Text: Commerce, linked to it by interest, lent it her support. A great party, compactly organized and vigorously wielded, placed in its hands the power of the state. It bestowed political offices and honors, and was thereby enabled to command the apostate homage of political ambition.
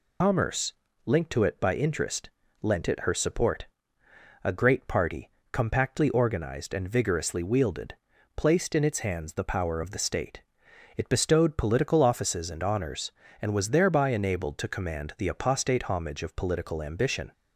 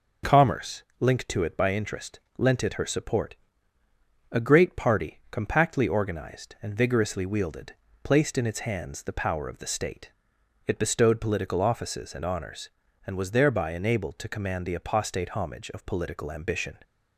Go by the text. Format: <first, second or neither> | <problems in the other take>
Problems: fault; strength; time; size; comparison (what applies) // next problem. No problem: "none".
second | loses the start of "Commerce"; at 0.2 s; 90 ms